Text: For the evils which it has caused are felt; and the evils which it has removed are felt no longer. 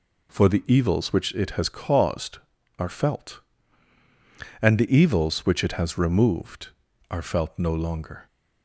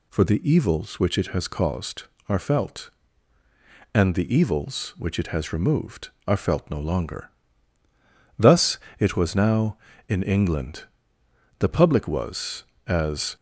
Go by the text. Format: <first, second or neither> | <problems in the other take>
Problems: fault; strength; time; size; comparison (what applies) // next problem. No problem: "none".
first | goes on to say "Thus it was now in England The public was as"; strong; from 8.3 s on; 5.0 s long